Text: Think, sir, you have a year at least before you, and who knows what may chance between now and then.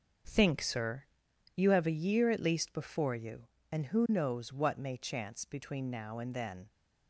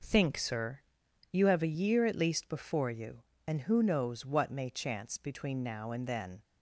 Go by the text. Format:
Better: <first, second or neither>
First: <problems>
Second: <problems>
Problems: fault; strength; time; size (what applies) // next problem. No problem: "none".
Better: second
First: gets quieter; strong; throughout; 9 dB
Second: none